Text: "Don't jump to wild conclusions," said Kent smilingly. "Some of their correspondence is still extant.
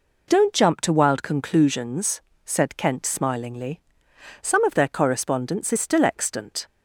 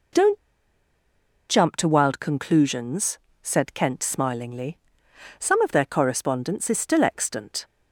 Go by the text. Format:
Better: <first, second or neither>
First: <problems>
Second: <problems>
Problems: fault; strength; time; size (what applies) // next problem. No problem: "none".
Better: first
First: none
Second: pauses between "Don't" and "jump"; at 0.3 s; 1.1 s long